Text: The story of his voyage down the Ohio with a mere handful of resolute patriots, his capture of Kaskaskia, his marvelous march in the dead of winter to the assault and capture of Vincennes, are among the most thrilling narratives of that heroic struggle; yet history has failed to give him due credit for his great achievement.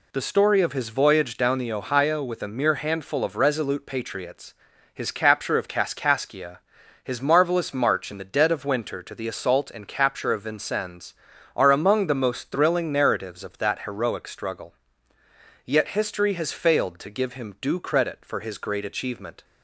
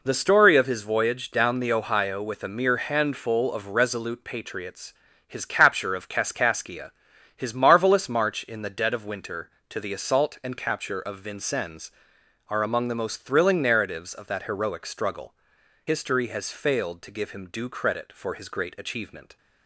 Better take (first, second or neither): first